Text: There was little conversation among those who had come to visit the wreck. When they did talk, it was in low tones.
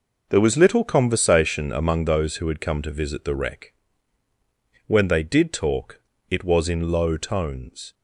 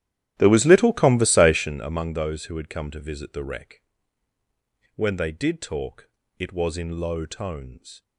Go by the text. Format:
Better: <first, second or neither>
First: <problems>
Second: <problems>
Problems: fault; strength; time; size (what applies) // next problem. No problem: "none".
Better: first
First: none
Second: starts louder than the rest; strong; until 1.8 s; 12.5 dB